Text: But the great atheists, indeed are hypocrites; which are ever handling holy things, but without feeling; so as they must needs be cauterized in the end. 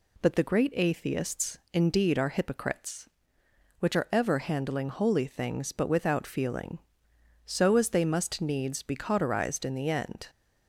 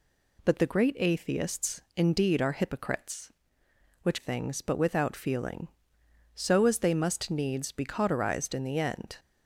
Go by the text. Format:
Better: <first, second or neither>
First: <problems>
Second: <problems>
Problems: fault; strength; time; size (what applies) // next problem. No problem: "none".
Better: first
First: none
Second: skips "are ever handling holy"; at 4.1 s